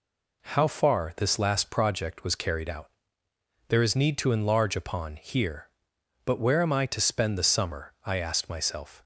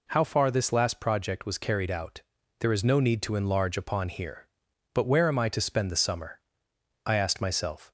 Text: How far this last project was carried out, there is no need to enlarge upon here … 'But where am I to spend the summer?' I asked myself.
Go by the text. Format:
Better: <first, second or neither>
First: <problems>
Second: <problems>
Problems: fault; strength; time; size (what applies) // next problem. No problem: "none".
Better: second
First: skips "no"; at 3.9 s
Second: none